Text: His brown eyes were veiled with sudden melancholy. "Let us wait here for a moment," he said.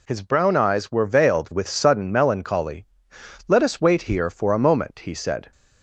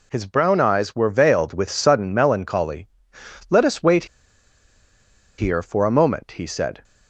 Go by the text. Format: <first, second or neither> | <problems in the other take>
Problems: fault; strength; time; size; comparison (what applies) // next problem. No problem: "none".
first | pauses between "wait" and "here"; strong; at 4.0 s; 1.3 s long